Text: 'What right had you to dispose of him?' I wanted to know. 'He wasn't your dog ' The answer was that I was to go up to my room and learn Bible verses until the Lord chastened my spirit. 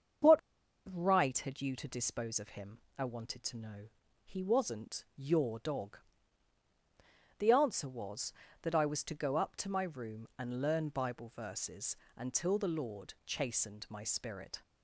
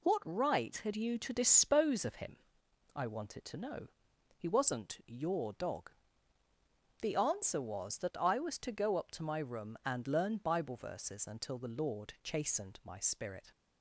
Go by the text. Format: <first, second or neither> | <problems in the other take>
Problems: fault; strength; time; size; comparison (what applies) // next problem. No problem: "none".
second | starts louder than the rest; strong; until 1.8 s; 7.5 dB // pauses between "What" and "right"; noticeable; at 0.3 s; 0.54 s long // pauses between "verses" and "until"; slight; at 11.9 s; 0.20 s long